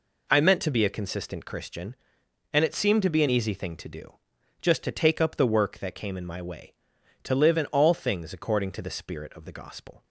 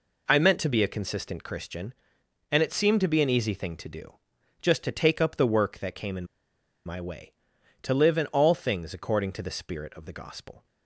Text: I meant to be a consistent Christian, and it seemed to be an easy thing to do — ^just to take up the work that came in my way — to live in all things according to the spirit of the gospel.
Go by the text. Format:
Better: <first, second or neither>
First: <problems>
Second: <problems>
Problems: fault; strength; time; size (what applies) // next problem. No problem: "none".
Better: first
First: none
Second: pauses between "in" and "my"; noticeable; at 6.2 s; 0.60 s long